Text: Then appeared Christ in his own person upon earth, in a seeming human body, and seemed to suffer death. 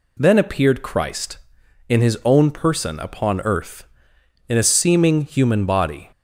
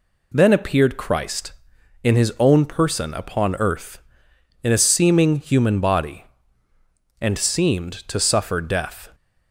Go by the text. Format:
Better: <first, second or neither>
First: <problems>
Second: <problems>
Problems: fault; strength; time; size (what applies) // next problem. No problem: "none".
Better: second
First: stops before "and seemed to suffer death"; at 6.1 s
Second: none